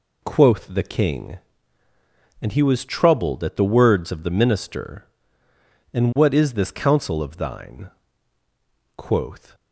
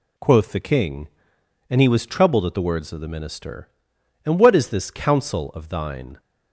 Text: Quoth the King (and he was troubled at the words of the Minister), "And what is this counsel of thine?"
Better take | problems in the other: second | goes on to say "Quoth"; from 8.9 s on; 0.58 s long

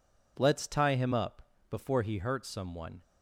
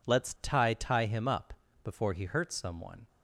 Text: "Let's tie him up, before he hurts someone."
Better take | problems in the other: first | says "tie" twice; at 0.7 s

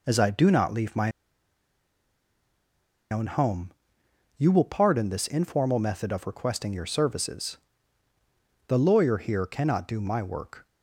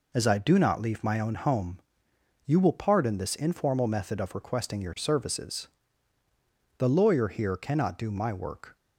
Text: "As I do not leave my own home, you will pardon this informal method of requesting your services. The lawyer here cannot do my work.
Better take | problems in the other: second | pauses between "my" and "own"; strong; at 1.1 s; 2.0 s long

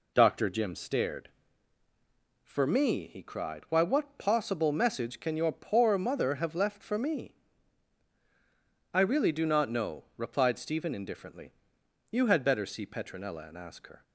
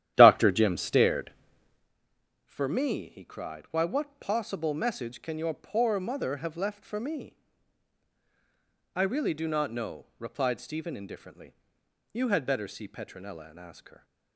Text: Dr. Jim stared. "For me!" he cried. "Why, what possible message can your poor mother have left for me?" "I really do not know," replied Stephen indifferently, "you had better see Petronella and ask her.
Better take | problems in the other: first | starts louder than the rest; strong; until 1.9 s; 11.5 dB

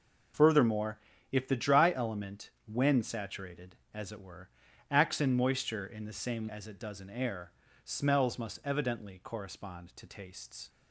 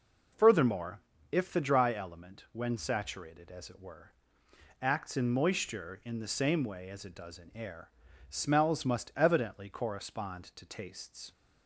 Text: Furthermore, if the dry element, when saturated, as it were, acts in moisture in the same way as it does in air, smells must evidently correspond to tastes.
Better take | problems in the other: second | skips "way"; at 6.4 s

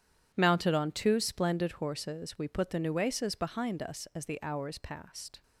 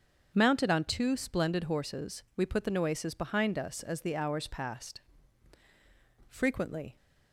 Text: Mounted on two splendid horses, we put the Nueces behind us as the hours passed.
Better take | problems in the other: first | starts louder than the rest; until 1.3 s; 7 dB // goes on to say "Frequently"; noticeable; from 6.2 s on; 0.68 s long

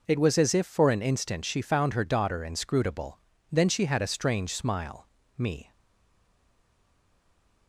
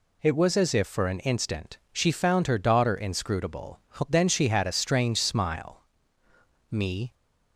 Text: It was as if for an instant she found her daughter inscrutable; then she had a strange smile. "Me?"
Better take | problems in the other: second | stays silent after the last word; noticeable; from 5.7 s on; 1.9 s long

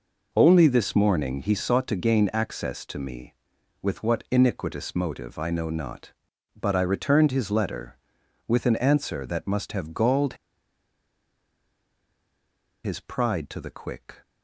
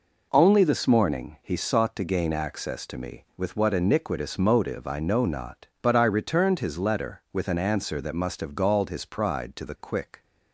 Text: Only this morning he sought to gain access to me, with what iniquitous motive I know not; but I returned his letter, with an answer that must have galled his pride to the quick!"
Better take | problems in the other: second | pauses between "galled" and "his"; strong; at 10.3 s; 2.5 s long

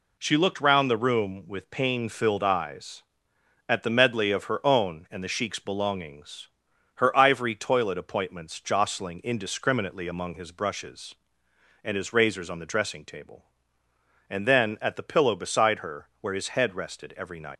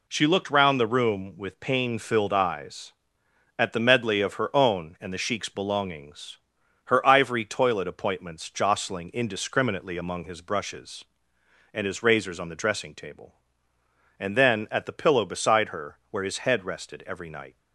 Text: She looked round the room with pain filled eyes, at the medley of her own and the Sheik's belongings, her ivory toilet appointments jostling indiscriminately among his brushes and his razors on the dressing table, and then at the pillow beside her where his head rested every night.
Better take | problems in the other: second | leaves "night" unfinished; at 17.5 s; 120 ms

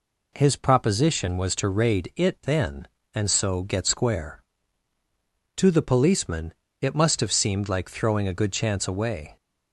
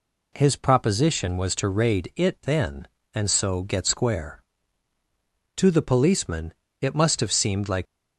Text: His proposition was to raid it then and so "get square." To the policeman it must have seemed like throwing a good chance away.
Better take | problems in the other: first | pauses between "policeman" and "it"; slight; at 6.5 s; 0.28 s long; slight in the first // stops before "throwing a good chance away"; at 7.8 s

